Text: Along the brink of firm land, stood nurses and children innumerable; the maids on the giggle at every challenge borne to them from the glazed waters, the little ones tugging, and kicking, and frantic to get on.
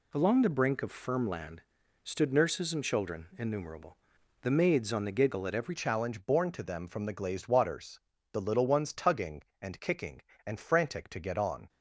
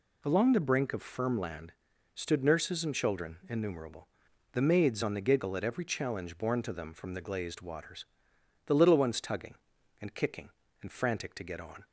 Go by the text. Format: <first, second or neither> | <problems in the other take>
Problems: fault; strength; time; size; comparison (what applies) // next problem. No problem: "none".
second | changes voice at "challenge"; from 5.7 s on; 5.9 s long